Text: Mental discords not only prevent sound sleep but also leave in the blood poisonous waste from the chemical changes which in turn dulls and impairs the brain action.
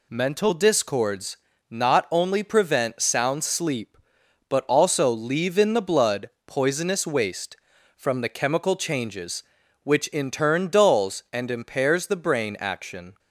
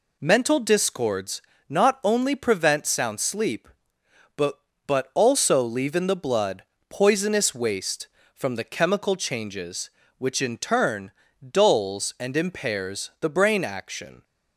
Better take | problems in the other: first | pauses between "discords" and "not"; slight; at 1.4 s; 0.28 s long; slight in the first // says "but" twice; at 4.8 s // pauses between "blood" and "poisonous"; slight; at 6.6 s; 0.26 s long; slight in the first // pauses between "turn" and "dulls"; at 11.1 s; 0.40 s long

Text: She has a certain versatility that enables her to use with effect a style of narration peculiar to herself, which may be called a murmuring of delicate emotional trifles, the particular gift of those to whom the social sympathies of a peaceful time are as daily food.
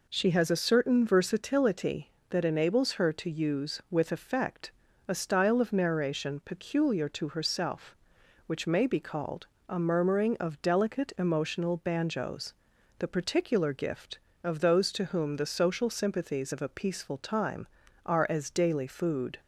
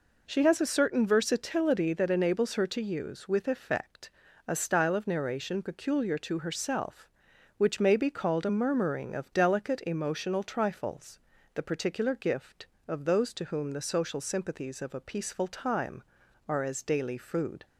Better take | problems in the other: second | pauses between "effect" and "a"; slight; at 4.7 s; 0.36 s long; also in the second // pauses between "called" and "a"; slight; at 9.4 s; 0.22 s long // says "banjos" for "trifles"; at 11.7 s

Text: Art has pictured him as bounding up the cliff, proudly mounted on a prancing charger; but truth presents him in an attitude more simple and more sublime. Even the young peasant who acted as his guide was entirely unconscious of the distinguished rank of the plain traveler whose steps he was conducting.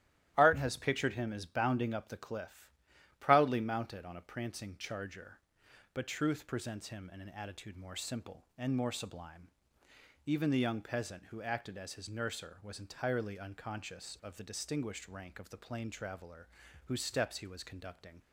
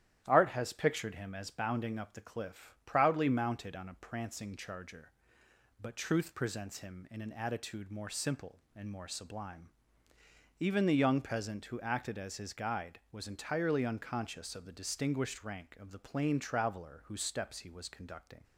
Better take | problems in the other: second | starts louder than the rest; strong; until 1.3 s; 13 dB; strong in the second // says "nurser" for "guide"; at 12.0 s // pauses between "traveler" and "whose"; slight; at 16.4 s; 0.36 s long

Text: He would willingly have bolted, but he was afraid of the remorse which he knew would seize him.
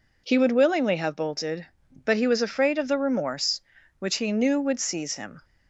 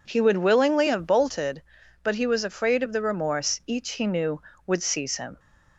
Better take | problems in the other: first | says "each" for "which"; at 3.6 s

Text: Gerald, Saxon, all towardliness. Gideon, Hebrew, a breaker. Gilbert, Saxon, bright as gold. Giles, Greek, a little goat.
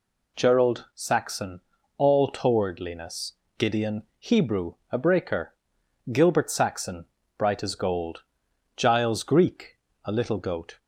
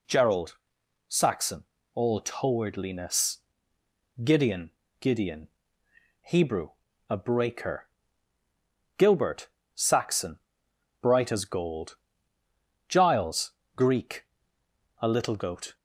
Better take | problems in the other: first | says "Gideon" twice; at 4.9 s

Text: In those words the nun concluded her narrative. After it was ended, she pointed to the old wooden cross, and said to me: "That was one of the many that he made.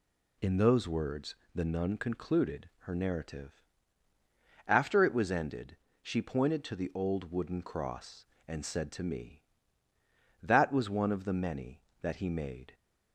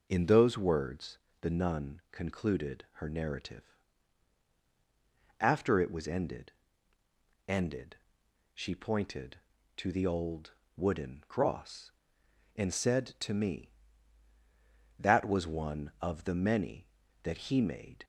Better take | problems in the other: first | pauses between "words" and "the"; slight; at 1.1 s; 0.22 s long; slight in the first // says "ended" twice; at 7.4 s // pauses between "old" and "wooden"; slight; at 10.5 s; 0.24 s long

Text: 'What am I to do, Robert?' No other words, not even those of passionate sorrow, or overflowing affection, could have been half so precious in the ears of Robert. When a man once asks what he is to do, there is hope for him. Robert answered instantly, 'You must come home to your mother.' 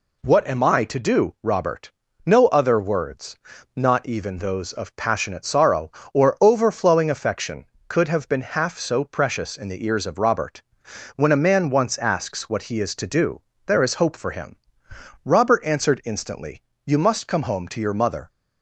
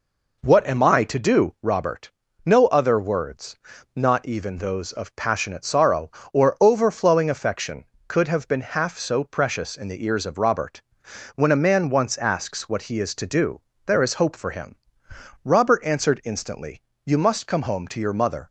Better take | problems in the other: first | starts louder than the rest; noticeable; until 1.7 s; 4.5 dB

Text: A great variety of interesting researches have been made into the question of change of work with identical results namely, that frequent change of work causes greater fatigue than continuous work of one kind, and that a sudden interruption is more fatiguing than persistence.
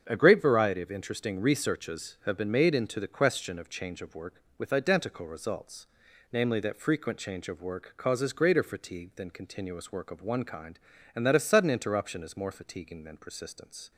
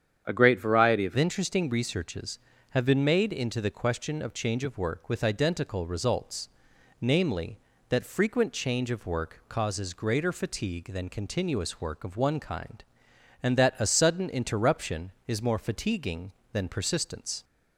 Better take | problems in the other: first | starts louder than the rest; strong; until 1.2 s; 8.5 dB; strong in the first // changes voice at "interesting"; from 1.1 s on; 16.3 s long // pauses between "results" and "namely"; noticeable; at 6.4 s; 0.52 s long; noticeable in the first

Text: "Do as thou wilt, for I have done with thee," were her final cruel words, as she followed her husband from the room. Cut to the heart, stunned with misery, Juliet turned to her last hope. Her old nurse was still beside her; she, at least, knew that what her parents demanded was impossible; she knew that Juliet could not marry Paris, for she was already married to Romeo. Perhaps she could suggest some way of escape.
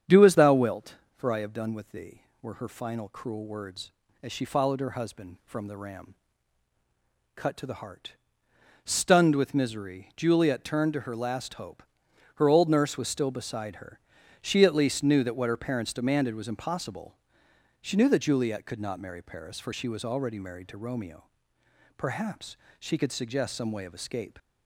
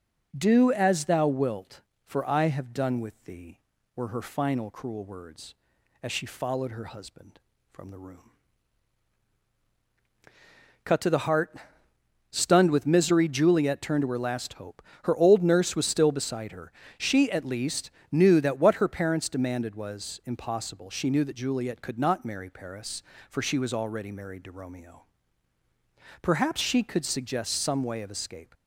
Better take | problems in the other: second | starts louder than the rest; strong; until 1.2 s; 8 dB // says "ram" for "room"; at 5.7 s // pauses between "Perhaps" and "she"; slight; at 22.5 s; 0.20 s long

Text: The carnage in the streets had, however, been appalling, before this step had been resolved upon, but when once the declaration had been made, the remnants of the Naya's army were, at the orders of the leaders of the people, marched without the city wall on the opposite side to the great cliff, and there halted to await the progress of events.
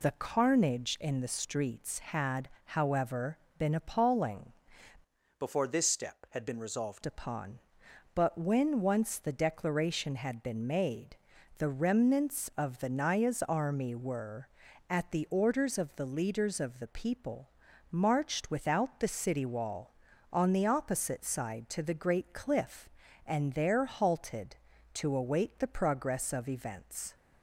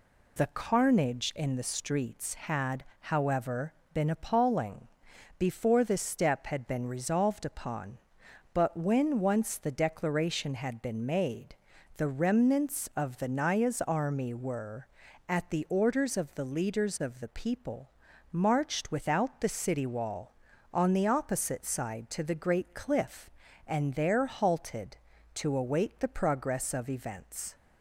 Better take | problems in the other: second | changes voice from "before" to "resolved"; from 5.3 to 7.0 s; 1.7 s long

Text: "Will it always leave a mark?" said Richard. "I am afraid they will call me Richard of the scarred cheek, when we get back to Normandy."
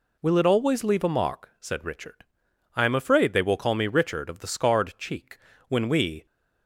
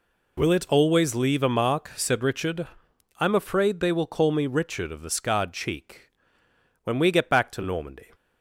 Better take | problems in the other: second | stops before "get back to Normandy"; at 6.2 s

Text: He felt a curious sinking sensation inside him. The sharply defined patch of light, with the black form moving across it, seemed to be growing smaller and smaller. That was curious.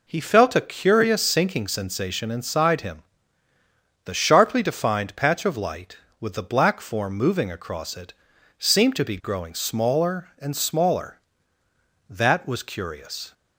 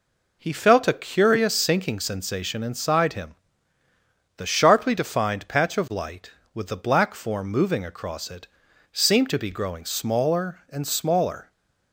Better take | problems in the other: first | stops before "That was curious"; at 11.5 s

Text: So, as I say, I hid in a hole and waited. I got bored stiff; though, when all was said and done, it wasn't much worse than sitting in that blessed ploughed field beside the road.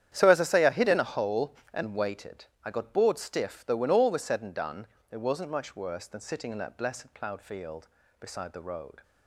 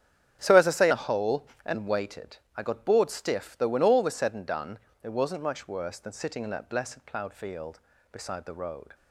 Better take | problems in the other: first | starts louder than the rest; strong; until 1.4 s; 9 dB; strong in the first // skips "I hid in"; at 0.9 s

